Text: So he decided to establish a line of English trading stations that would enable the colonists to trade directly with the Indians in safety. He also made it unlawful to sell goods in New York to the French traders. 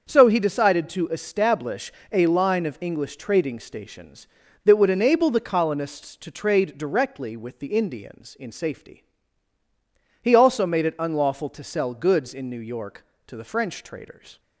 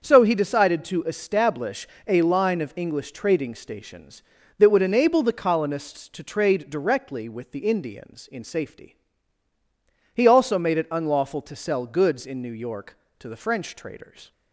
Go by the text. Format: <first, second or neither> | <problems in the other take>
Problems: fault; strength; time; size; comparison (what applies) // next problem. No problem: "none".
neither | starts louder than the rest; the same in both // pauses between "establish" and "a"; slight; the same in both